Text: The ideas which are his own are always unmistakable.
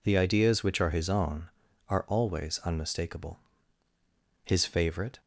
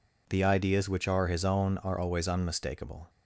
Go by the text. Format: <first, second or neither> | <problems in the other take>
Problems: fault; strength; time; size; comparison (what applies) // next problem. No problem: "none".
second | goes on to say "His favourite"; noticeable; from 4.4 s on; 0.76 s long